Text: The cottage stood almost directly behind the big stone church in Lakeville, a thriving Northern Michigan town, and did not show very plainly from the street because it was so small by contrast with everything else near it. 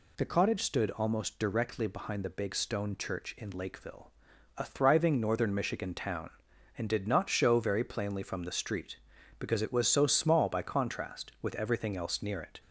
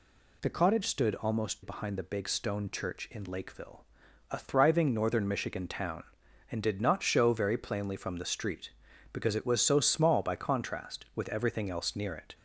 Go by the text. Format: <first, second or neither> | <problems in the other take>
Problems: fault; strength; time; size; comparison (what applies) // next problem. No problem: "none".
first | skips "directly"; at 1.6 s